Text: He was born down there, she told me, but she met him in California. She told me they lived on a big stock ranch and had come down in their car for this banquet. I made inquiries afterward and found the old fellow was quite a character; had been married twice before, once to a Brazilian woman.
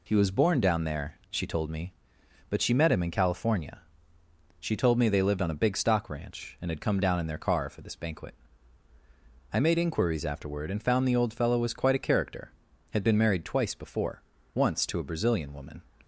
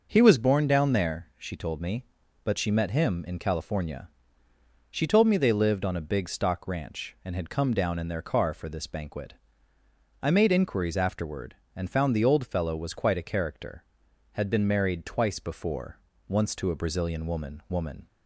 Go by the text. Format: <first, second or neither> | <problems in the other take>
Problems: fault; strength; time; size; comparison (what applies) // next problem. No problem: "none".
first | says "woman" twice; at 17.6 s